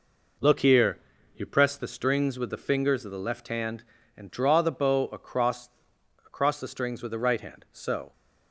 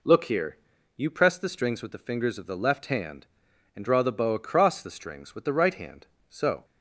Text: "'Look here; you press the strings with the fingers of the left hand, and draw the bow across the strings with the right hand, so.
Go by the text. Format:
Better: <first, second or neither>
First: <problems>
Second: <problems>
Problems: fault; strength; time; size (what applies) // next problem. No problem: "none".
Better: second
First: says "across" twice; at 6.2 s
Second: none